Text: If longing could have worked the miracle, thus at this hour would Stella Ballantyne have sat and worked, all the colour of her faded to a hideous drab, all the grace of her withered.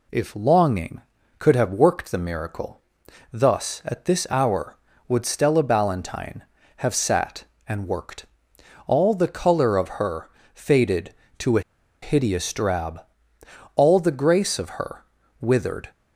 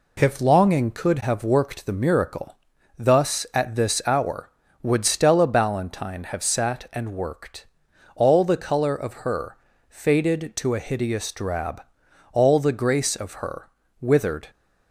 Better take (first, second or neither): second